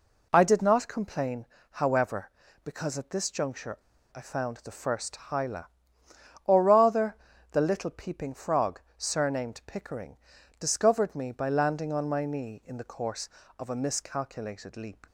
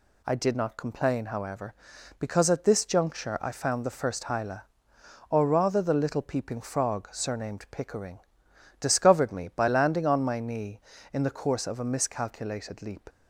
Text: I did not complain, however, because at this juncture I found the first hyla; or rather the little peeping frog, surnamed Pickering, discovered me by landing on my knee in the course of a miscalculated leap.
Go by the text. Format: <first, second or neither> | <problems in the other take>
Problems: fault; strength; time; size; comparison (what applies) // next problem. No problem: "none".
second | pauses between "juncture" and "I"; at 3.7 s; 0.37 s long // pauses between "rather" and "the"; at 7.1 s; 0.38 s long